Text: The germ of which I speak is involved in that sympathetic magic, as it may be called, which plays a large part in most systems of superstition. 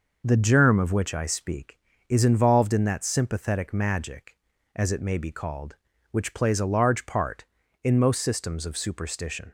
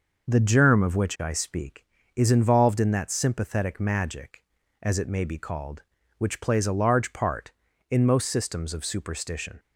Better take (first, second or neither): neither